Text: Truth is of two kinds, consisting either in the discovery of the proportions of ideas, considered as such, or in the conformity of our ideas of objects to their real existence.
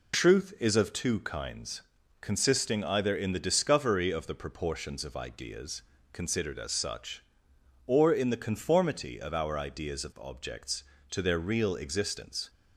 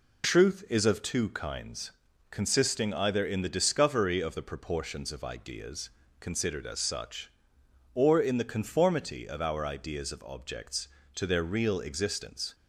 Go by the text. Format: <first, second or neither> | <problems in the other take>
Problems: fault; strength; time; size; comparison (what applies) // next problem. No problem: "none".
neither | none